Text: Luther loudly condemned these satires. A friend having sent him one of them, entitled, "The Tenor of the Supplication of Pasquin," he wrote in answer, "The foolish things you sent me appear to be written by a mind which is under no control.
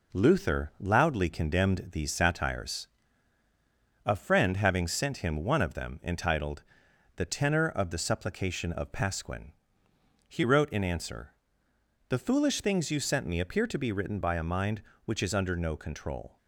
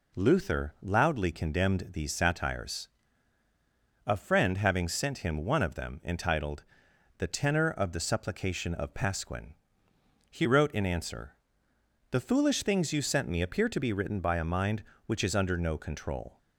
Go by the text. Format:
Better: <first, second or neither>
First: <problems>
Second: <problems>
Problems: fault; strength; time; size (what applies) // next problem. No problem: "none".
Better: second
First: gets quieter; slight; throughout; 3 dB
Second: none